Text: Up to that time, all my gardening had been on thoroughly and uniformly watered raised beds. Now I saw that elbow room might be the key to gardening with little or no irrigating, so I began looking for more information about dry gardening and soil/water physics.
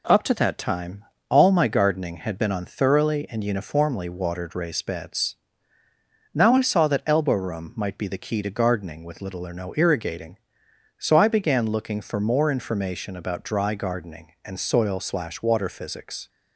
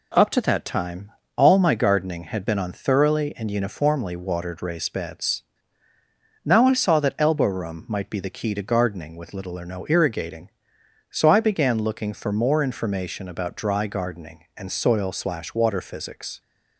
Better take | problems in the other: neither | none

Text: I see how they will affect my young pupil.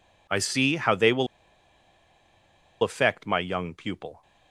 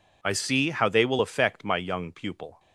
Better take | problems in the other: second | pauses between "will" and "affect"; strong; at 1.2 s; 1.5 s long

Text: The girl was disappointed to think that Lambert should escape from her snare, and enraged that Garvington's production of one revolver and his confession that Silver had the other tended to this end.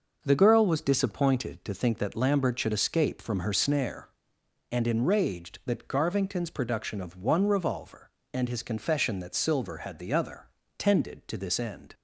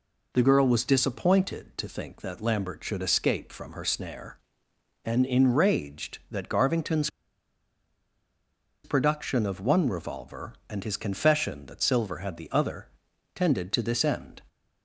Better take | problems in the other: first | pauses between "Garvington's" and "production"; strong; at 7.0 s; 1.7 s long // pauses between "other" and "tended"; noticeable; at 12.8 s; 0.48 s long; slight in the first

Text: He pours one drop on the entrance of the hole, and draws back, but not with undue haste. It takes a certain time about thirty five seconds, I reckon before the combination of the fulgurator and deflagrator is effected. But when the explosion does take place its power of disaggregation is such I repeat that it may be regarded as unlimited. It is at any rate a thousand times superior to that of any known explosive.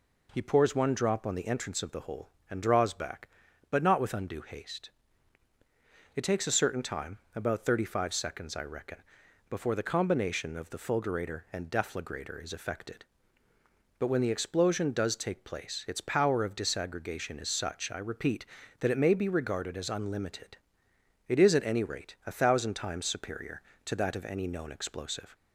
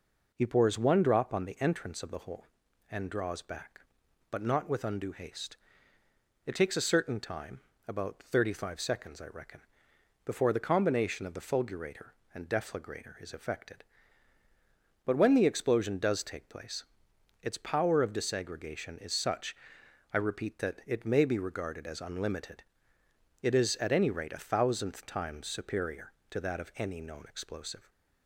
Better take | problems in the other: first | pauses between "time" and "about"; slight; at 7.6 s; 0.26 s long; slight in the first // pauses between "reckon" and "before"; noticeable; at 9.6 s; 0.64 s long; noticeable in the first // pauses between "place" and "its"; noticeable; at 16.8 s; 0.58 s long // pauses between "such" and "I"; noticeable; at 19.5 s; 0.56 s long // says "thousandth" for "thousand"; at 24.4 s

